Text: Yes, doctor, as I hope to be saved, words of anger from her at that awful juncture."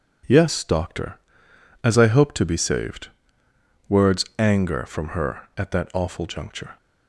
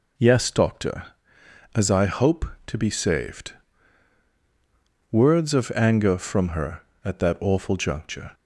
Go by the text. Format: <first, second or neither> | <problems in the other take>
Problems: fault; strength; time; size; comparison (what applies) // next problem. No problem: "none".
second | skips "of"; at 4.3 s